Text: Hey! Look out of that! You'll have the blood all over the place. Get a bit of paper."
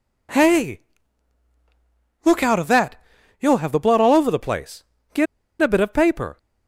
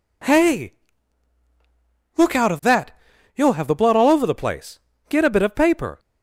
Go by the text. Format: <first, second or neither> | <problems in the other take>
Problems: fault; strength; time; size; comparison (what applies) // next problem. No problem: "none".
second | pauses between "Get" and "a"; slight; at 5.2 s; 0.35 s long